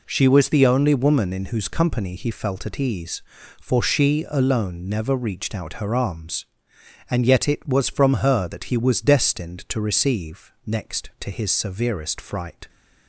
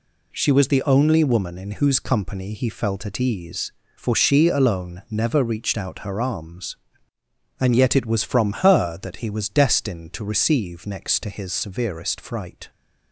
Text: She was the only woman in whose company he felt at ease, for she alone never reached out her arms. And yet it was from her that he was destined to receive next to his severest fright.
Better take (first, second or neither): neither